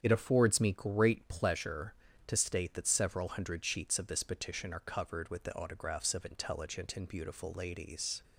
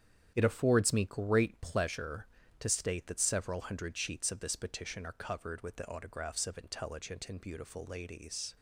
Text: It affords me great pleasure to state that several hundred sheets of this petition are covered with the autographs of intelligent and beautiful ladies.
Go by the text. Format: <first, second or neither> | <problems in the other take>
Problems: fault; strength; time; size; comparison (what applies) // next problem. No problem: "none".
first | gets quieter; strong; throughout; 9 dB // starts louder than the rest; strong; until 1.3 s; 9 dB; strong in the first